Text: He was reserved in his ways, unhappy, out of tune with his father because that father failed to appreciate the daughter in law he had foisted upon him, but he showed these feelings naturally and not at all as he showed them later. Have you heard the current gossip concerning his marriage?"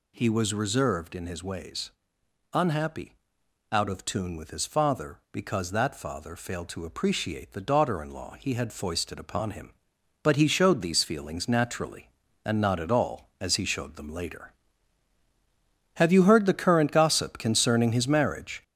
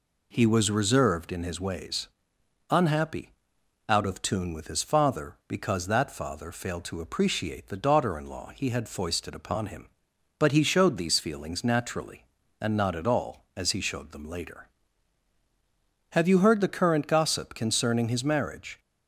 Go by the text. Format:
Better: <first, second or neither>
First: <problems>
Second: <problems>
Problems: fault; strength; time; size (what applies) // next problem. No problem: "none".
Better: second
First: gets louder; noticeable; throughout; 5.5 dB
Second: none